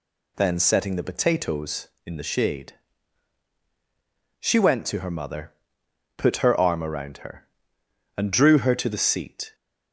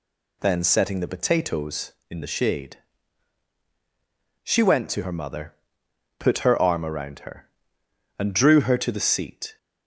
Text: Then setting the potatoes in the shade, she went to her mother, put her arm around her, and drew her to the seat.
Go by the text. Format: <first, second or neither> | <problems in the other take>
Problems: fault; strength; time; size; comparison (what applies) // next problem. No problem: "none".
neither | none